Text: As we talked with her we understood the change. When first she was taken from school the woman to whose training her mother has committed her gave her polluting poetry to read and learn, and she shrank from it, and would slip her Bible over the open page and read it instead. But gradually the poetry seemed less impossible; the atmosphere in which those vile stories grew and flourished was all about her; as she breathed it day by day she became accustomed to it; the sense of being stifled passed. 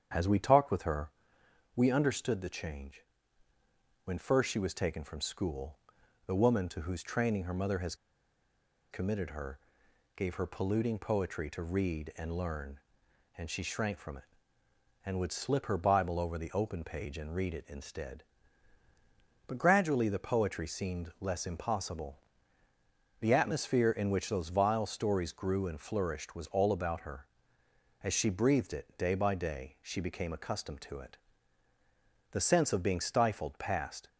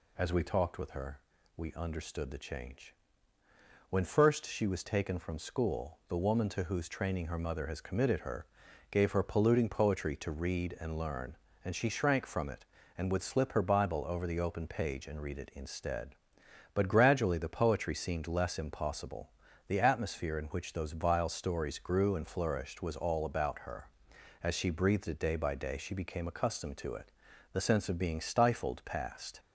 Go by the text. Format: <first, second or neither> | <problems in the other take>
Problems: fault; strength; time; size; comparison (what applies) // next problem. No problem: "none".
second | starts louder than the rest; strong; until 1.7 s; 8 dB // pauses between "her" and "we"; noticeable; at 1.1 s; 0.64 s long; also in the second // pauses between "school" and "the"; noticeable; at 5.7 s; 0.48 s long // pauses between "has" and "committed"; noticeable; at 7.9 s; 0.97 s long // pauses between "her" and "gave"; noticeable; at 9.6 s; 0.56 s long; noticeable in the second